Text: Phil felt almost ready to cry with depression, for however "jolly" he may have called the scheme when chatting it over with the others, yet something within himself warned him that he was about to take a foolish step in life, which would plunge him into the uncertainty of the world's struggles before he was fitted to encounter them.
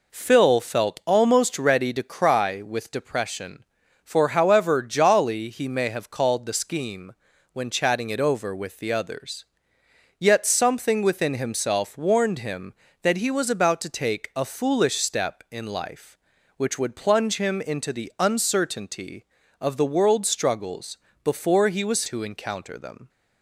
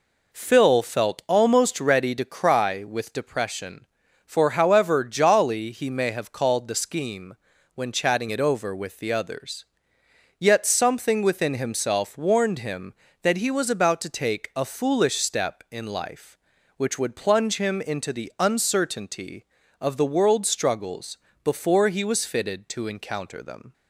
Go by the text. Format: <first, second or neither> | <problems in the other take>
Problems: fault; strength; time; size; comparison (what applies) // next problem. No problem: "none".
second | pauses between "scheme" and "when"; at 7.1 s; 0.40 s long; also in the second // pauses between "struggles" and "before"; slight; at 20.9 s; 0.26 s long; slight in the second // skips "fitted"; at 22.0 s